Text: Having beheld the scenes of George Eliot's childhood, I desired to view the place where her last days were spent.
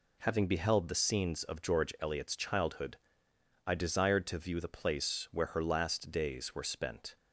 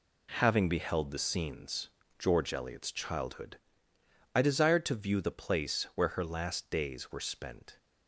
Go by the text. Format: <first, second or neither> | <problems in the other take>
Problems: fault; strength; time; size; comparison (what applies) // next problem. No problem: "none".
first | skips "of"; at 2.0 s